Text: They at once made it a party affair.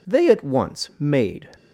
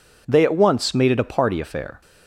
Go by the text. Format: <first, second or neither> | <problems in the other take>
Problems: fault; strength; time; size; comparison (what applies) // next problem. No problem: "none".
second | stops before "it a party affair"; at 1.5 s